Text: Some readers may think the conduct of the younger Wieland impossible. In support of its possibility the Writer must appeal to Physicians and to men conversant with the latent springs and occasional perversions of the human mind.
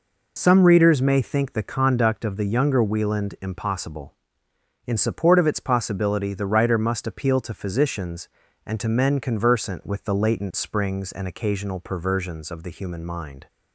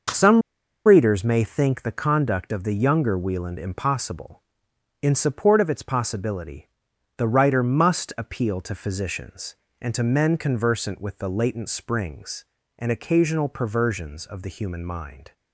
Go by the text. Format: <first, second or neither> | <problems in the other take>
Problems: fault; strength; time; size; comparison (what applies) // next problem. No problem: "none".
first | starts louder than the rest; noticeable; until 1.5 s; 6 dB // pauses between "Some" and "readers"; at 0.4 s; 0.45 s long // pauses between "possibility" and "the"; noticeable; at 6.6 s; 0.48 s long